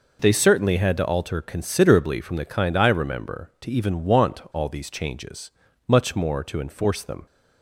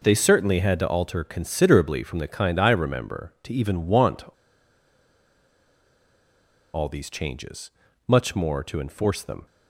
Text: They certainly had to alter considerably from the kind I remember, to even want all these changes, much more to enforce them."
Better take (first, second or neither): first